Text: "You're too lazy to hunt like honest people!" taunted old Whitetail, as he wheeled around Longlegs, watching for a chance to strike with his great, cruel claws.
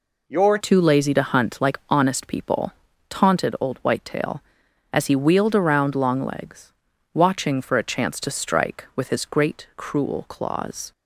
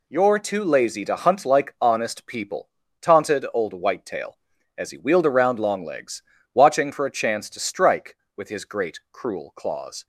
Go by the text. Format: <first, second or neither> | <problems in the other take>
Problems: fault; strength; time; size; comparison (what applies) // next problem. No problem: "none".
second | changes voice at "too"; from 0.5 s on; 10.4 s long